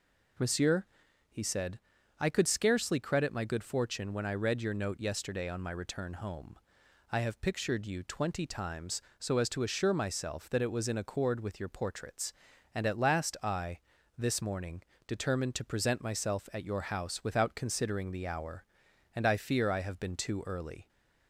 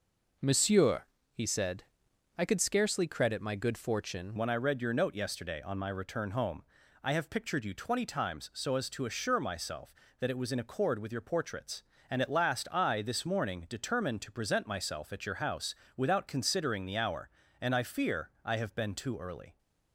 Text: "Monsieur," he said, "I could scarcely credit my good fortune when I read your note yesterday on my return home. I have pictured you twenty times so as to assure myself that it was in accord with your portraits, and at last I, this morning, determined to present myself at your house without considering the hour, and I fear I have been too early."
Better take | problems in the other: first | changes voice at "when"; from 4.3 s on; 15.2 s long // pauses between "house" and "without"; slight; at 15.7 s; 0.24 s long // pauses between "fear" and "I"; slight; at 18.2 s; 0.16 s long

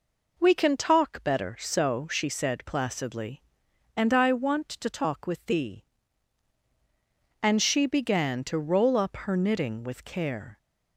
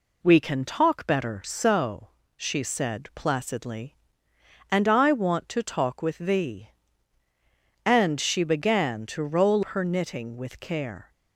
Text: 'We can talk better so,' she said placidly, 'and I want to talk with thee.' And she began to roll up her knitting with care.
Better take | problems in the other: first | skips "up"; at 9.6 s

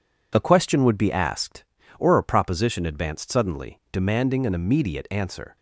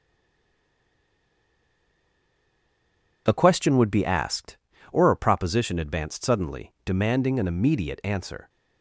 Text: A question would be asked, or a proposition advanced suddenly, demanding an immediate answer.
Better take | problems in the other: first | stays silent before the first word; strong; until 3.2 s; 3.2 s long

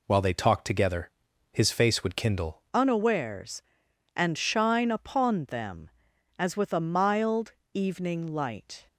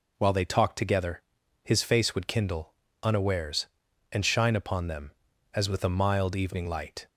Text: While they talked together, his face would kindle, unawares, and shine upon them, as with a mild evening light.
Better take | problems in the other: second | changes voice at "unawares"; from 2.7 s on; 6.1 s long // pauses between "mild" and "evening"; slight; at 7.5 s; 0.20 s long

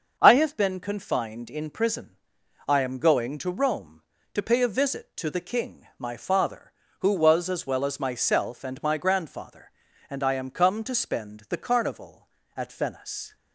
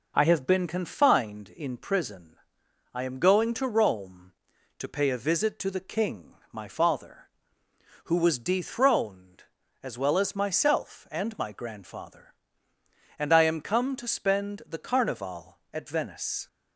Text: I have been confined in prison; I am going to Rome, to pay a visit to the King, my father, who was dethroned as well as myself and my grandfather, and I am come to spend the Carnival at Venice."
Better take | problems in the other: second | starts louder than the rest; until 1.2 s; 6.5 dB // skips "dethroned"; at 7.4 s

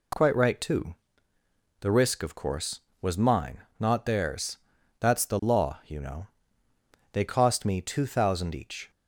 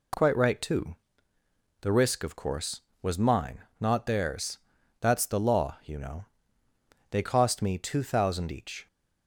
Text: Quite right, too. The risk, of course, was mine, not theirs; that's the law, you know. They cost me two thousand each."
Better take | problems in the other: neither | none

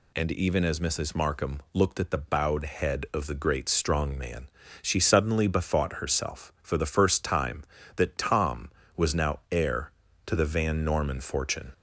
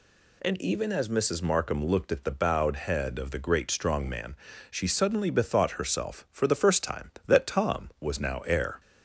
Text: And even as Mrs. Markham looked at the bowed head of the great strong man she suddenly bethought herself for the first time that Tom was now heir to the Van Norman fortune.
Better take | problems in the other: first | pauses between "man" and "she"; slight; at 4.3 s; 0.34 s long; slight in the first // stops before "to the Van Norman fortune"; at 8.7 s

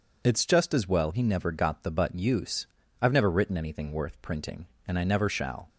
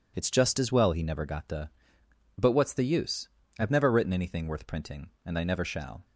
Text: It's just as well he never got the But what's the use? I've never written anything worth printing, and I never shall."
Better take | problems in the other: second | skips "what's the"; at 2.1 s

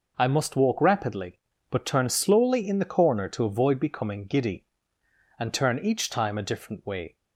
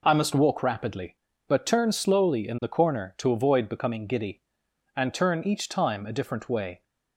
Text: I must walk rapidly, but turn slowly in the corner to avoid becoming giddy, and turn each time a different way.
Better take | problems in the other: neither | none

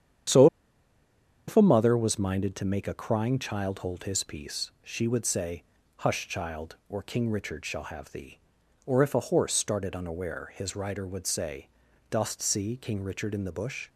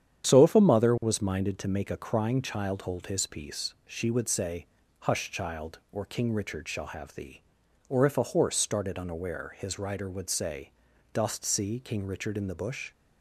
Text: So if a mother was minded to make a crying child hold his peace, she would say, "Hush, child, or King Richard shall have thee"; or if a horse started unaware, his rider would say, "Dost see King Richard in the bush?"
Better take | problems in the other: second | starts louder than the rest; strong; until 2.3 s; 9 dB; strong in the second // pauses between "So" and "if"; at 0.4 s; 1.0 s long

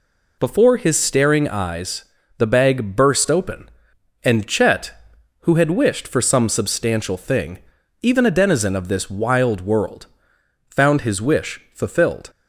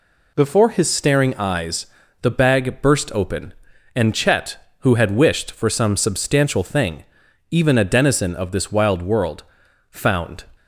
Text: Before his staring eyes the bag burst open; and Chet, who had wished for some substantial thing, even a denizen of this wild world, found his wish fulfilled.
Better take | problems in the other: first | pauses between "eyes" and "the"; slight; at 1.8 s; 0.36 s long; slight in the first // stops before "his wish fulfilled"; at 10.5 s

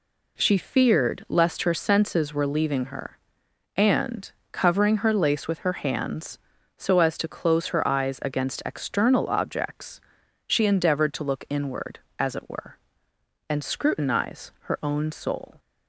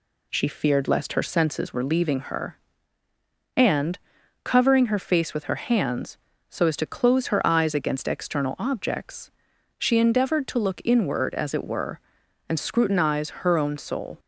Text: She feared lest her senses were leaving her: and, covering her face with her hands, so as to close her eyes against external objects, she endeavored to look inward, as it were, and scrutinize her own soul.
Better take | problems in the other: second | says "lace" for "face"; at 5.1 s

